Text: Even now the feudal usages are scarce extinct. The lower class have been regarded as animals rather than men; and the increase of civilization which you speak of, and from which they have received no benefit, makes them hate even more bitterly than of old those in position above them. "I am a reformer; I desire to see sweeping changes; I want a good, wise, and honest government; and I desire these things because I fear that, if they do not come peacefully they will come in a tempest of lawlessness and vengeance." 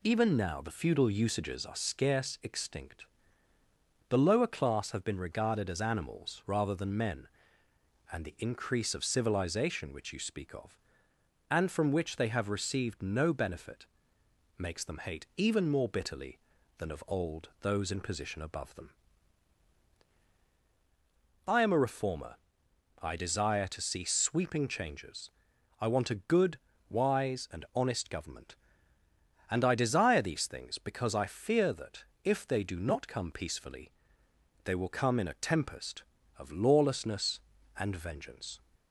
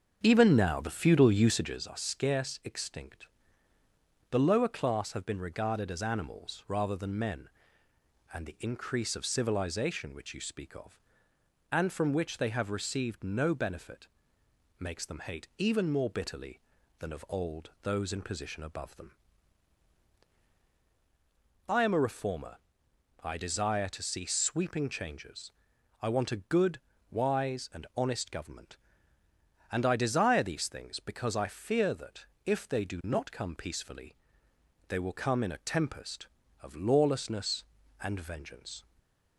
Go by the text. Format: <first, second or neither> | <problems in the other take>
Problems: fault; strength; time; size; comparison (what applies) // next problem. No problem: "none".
first | starts louder than the rest; strong; until 1.8 s; 7 dB // pauses between "peacefully" and "they"; noticeable; at 34.1 s; 0.74 s long; noticeable in the first // stays silent after the last word; slight; from 38.8 s on; 0.5 s long